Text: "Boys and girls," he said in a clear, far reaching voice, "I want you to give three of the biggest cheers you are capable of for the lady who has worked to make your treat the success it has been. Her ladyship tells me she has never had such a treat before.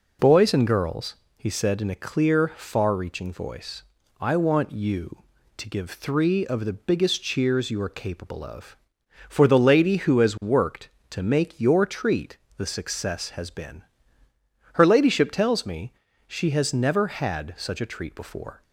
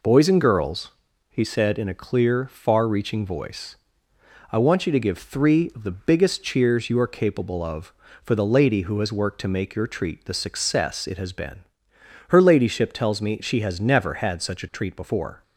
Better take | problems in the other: second | pauses between "treat" and "the"; slight; at 12.3 s; 0.18 s long // skips "it"; at 13.2 s // pauses between "me" and "she"; slight; at 15.9 s; 0.34 s long

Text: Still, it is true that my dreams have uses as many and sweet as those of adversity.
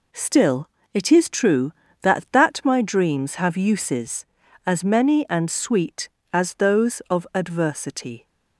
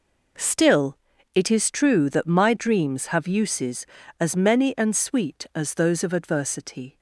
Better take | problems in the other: second | says "that" twice; at 2.3 s

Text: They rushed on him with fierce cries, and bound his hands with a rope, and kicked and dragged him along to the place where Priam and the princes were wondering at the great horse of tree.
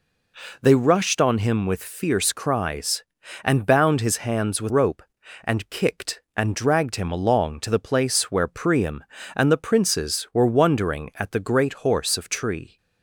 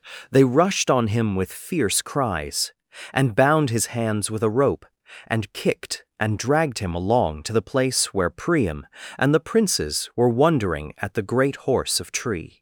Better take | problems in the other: second | skips "a"; at 4.7 s

